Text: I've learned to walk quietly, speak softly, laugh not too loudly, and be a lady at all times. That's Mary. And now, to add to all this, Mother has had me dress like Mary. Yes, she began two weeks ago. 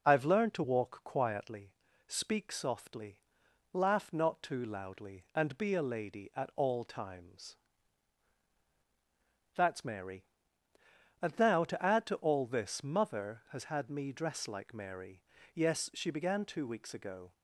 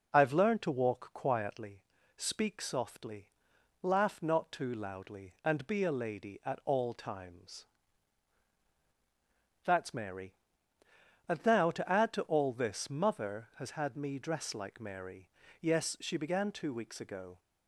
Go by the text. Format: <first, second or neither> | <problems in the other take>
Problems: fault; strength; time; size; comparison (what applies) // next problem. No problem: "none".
neither | none